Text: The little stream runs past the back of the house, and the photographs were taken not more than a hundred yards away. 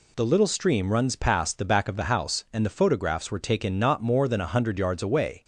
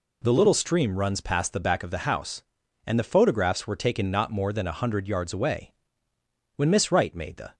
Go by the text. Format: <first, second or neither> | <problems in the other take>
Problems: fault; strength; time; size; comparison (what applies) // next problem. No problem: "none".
first | goes on to say "When Miss Wright made the"; noticeable; from 6.5 s on; 1.0 s long